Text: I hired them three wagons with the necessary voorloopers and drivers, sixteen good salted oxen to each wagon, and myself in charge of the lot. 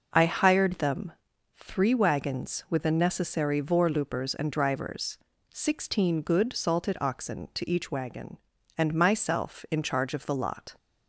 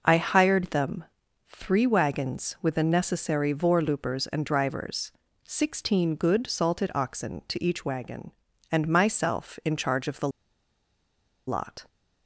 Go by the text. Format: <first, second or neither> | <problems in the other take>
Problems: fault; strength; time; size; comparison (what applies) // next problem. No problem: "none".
first | pauses between "them" and "three"; at 1.0 s; 0.44 s long; also in the first // pauses between "the" and "lot"; at 10.2 s; 1.1 s long